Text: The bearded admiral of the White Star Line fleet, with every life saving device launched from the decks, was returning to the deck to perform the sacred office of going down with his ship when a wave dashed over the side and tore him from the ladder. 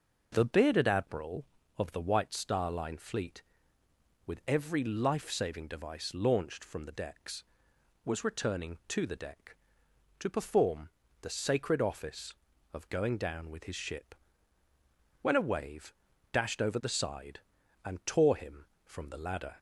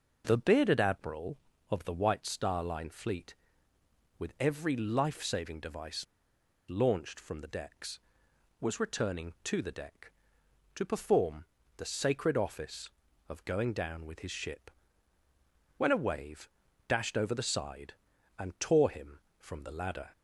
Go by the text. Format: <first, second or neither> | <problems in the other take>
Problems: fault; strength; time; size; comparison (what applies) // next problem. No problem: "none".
first | pauses between "device" and "launched"; noticeable; at 6.0 s; 0.67 s long // pauses between "perform" and "the"; slight; at 11.4 s; 0.32 s long; slight in the first // pauses between "ship" and "when"; at 14.7 s; 1.0 s long; also in the first // pauses between "wave" and "dashed"; at 16.4 s; 0.38 s long; also in the first